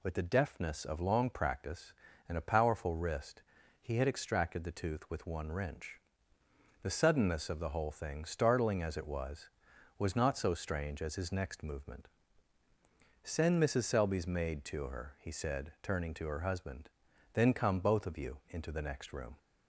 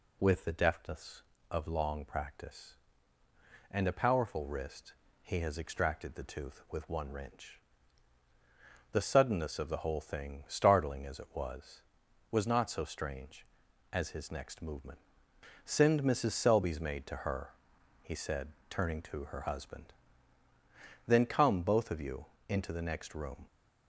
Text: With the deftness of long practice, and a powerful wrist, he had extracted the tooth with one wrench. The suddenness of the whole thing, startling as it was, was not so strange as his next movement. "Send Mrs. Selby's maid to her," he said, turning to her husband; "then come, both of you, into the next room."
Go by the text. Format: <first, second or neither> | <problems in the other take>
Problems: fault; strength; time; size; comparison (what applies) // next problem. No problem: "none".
first | says "has" for "had"; at 5.4 s